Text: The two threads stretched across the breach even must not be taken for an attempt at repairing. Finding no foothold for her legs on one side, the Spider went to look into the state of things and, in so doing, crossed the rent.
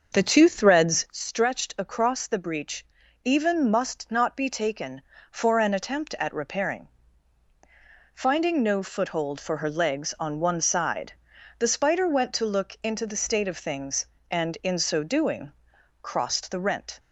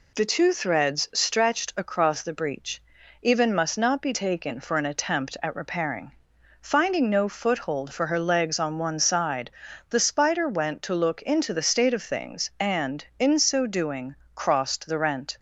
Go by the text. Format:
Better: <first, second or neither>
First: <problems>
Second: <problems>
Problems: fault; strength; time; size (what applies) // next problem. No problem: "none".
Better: second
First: starts louder than the rest; until 1.1 s; 6.5 dB // pauses between "breach" and "even"; at 2.8 s; 0.40 s long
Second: pauses between "breach" and "even"; at 2.8 s; 0.38 s long